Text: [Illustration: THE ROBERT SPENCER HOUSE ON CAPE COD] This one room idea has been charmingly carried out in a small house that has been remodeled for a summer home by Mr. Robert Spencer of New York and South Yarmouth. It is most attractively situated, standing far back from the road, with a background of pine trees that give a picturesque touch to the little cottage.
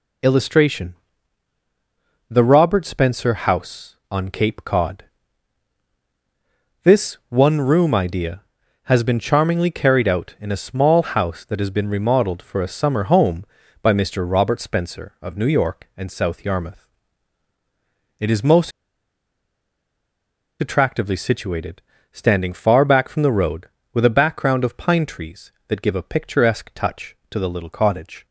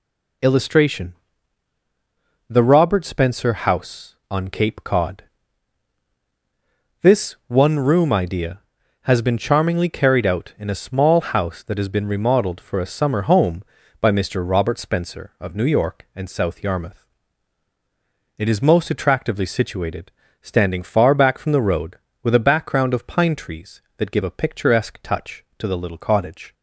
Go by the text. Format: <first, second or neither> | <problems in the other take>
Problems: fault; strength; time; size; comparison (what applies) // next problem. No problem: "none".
second | pauses between "COD" and "This"; strong; at 5.0 s; 1.7 s long; strong in the second // pauses between "most" and "attractively"; strong; at 18.7 s; 1.9 s long